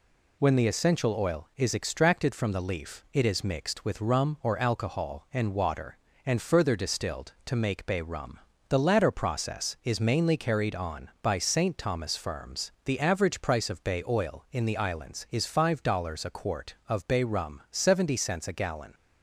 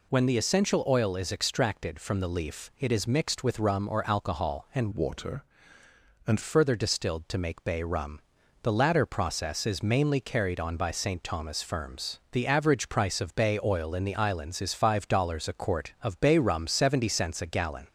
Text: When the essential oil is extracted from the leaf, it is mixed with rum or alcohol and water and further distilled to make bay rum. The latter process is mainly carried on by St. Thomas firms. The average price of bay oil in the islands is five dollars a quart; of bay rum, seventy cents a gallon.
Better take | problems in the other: first | changes voice from "water" to "and"; from 4.9 to 6.4 s; 1.5 s long

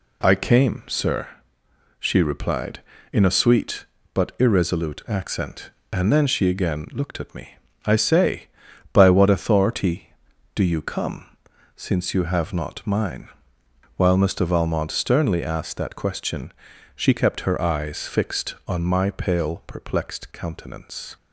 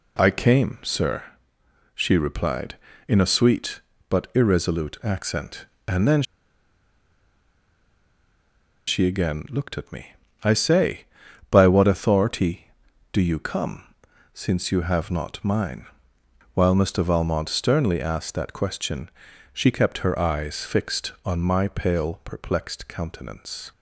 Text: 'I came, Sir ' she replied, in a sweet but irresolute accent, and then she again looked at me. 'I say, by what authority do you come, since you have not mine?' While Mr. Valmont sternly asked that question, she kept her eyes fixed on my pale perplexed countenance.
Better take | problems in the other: first | pauses between "then" and "she"; strong; at 6.2 s; 2.6 s long

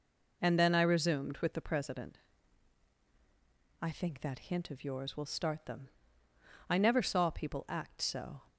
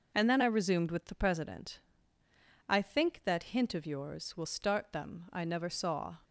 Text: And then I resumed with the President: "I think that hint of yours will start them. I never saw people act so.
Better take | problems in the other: first | stops before "people act so"; at 6.2 s

